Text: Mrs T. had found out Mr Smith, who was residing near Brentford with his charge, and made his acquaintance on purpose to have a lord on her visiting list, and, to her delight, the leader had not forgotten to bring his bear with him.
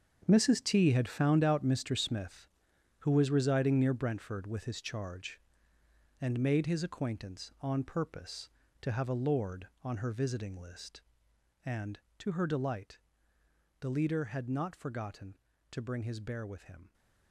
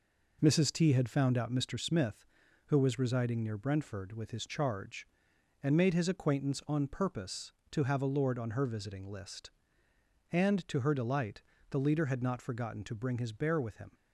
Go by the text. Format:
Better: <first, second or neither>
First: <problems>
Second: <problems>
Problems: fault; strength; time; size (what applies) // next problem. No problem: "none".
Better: second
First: gets quieter; strong; throughout; 12 dB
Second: none